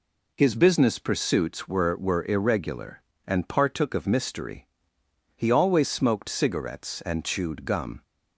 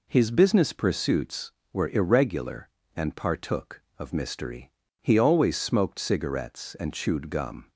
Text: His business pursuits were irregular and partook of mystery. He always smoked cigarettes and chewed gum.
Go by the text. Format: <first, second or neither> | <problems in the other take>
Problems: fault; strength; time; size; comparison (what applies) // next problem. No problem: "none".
second | says "were" twice; at 1.9 s